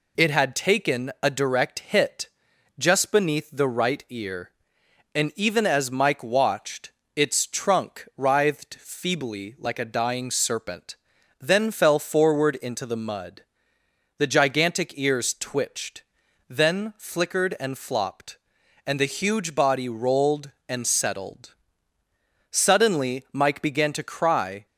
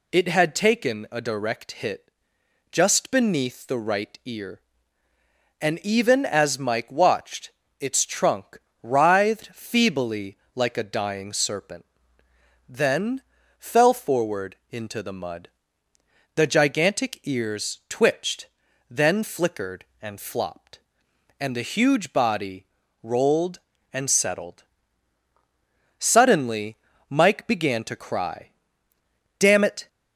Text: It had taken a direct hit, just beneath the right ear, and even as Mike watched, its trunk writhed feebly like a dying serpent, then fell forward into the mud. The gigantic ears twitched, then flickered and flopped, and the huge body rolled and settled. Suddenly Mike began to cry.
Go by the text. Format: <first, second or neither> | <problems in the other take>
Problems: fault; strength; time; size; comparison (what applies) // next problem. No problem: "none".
first | pauses between "trunk" and "writhed"; slight; at 8.5 s; 0.24 s long // pauses between "feebly" and "like"; slight; at 10.3 s; 0.18 s long // pauses between "then" and "fell"; at 13.2 s; 0.38 s long // pauses between "body" and "rolled"; slight; at 22.6 s; 0.36 s long // pauses between "Suddenly" and "Mike"; slight; at 26.7 s; 0.34 s long // goes on to say "Damn it"; slight; from 29.3 s on; 0.48 s long